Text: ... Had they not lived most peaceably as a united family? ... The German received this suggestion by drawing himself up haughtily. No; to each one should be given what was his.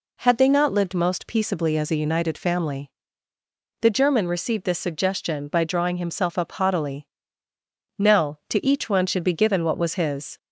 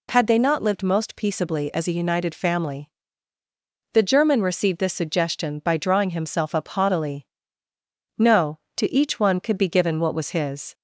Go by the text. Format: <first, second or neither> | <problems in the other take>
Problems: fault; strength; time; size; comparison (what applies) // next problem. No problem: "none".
first | says "could" for "should"; at 9.3 s